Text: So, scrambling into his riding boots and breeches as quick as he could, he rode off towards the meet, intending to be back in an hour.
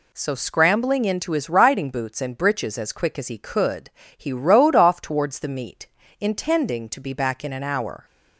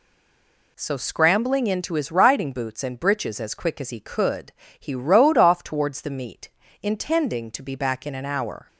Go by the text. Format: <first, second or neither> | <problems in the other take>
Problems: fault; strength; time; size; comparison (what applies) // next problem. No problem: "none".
first | stays silent before the first word; slight; until 0.7 s; 0.7 s long